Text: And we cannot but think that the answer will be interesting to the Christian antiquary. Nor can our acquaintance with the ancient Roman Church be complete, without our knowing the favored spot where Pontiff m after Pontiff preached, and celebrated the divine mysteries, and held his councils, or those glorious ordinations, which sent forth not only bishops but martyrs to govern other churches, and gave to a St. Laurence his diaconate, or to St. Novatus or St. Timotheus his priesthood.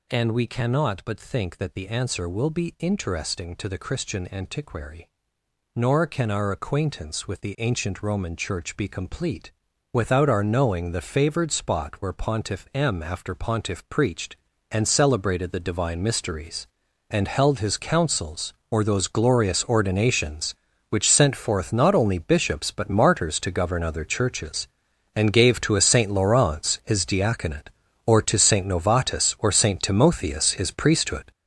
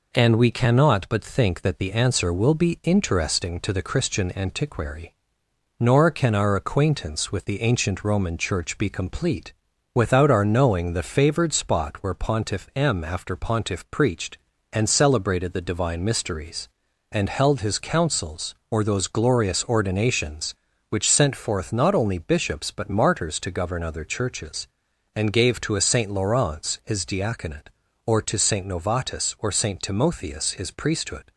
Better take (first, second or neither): second